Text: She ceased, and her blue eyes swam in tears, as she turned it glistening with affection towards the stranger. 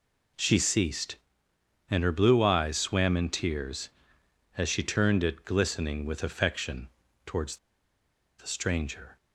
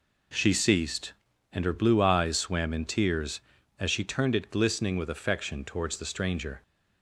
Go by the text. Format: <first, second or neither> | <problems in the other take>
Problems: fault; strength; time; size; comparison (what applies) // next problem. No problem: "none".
second | pauses between "affection" and "towards"; slight; at 6.8 s; 0.36 s long // pauses between "towards" and "the"; noticeable; at 7.5 s; 0.81 s long